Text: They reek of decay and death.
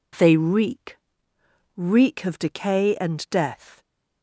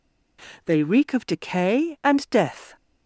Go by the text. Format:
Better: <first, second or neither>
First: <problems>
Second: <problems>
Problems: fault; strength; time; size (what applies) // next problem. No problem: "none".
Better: second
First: says "reek" twice; at 1.7 s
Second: none